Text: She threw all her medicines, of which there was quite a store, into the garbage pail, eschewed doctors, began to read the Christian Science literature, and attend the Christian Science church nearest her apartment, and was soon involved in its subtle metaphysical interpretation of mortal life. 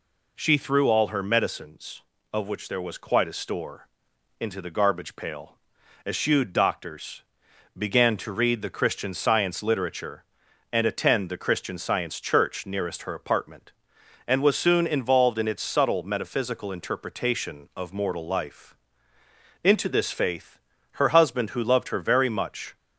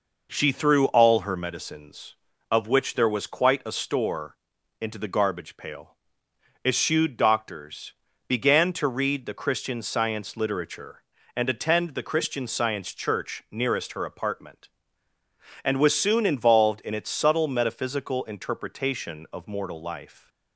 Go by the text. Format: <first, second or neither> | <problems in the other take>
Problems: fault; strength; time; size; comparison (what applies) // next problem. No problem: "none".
second | goes on to say "Into this faith her husband who loved her very much"; strong; from 19.6 s on; 3.1 s long